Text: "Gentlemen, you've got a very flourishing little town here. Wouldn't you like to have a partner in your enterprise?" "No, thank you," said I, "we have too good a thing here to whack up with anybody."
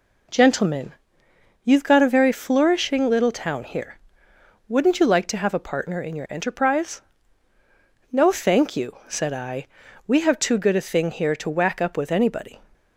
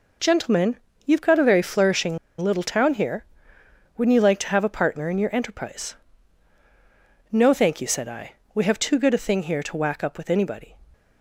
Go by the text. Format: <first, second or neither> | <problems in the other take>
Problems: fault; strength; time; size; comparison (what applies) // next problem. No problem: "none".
first | pauses between "flourishing" and "little"; slight; at 2.1 s; 0.21 s long